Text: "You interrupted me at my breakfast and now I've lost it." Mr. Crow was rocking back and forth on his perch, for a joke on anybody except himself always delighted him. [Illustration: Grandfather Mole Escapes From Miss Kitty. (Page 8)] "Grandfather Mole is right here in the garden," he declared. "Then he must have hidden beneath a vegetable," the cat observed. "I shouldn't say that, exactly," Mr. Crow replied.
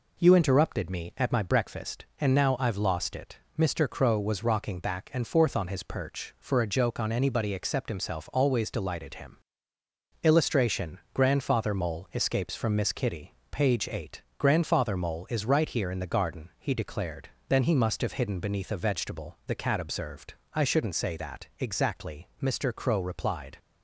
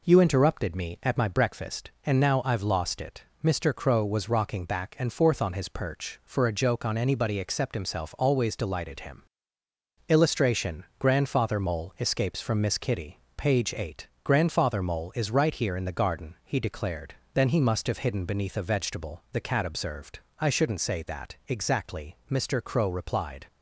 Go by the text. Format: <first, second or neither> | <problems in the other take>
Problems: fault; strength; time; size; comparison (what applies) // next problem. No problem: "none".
neither | none